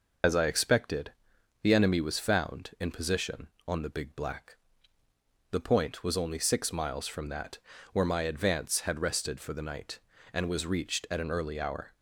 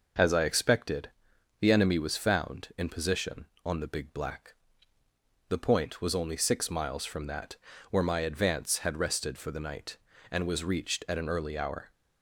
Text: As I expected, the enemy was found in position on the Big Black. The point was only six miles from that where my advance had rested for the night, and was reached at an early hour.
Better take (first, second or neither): second